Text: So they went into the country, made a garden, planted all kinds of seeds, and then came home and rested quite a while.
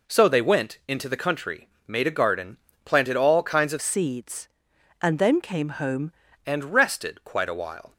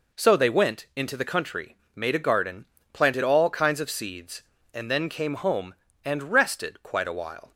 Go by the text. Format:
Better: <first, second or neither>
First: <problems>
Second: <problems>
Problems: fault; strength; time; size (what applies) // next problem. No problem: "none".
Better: second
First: changes voice from "seeds" to "home"; from 3.8 to 6.1 s; 2.3 s long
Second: none